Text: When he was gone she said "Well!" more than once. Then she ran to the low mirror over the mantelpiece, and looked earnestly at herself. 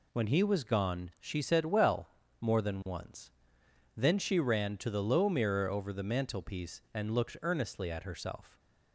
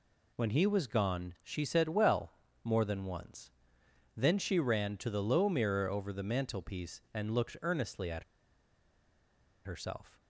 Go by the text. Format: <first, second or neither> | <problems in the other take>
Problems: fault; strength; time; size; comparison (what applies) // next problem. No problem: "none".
first | pauses between "at" and "herself"; strong; at 8.2 s; 1.4 s long